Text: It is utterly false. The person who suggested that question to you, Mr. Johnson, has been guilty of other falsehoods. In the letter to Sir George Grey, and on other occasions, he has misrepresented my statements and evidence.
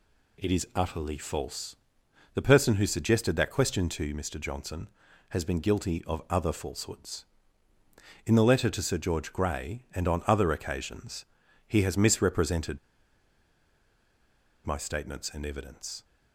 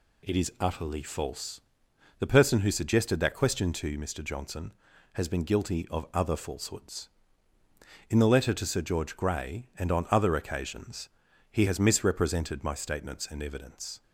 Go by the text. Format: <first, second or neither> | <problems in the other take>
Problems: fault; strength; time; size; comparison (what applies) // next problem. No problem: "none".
second | pauses between "misrepresented" and "my"; strong; at 12.7 s; 1.8 s long